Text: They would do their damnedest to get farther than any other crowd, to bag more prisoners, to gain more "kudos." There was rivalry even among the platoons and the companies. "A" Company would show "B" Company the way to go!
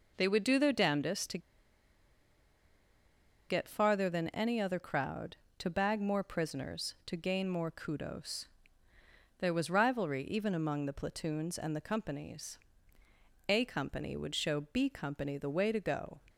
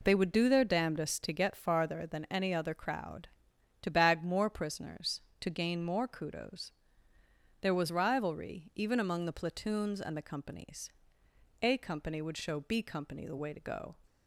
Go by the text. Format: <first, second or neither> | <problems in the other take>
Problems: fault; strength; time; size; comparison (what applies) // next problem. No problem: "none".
second | pauses between "to" and "get"; strong; at 1.3 s; 2.1 s long